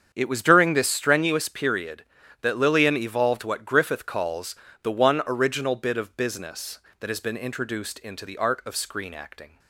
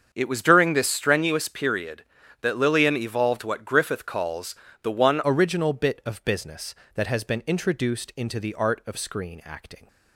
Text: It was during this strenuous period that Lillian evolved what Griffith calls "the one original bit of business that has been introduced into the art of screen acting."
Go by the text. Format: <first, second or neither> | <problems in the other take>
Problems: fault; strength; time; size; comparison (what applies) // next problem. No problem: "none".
first | starts louder than the rest; until 1.1 s; 7 dB; strong in the first // pauses between "calls" and "the"; slight; at 4.5 s; 0.28 s long; slight in the first // changes voice at "original"; from 5.2 s on; 4.6 s long